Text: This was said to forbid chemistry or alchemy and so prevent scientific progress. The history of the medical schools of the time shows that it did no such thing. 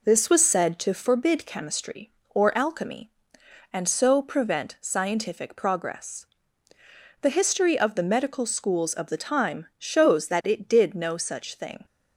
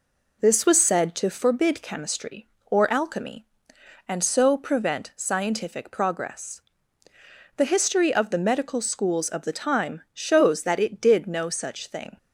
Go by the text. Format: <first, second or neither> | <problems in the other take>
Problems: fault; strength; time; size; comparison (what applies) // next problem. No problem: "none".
neither | none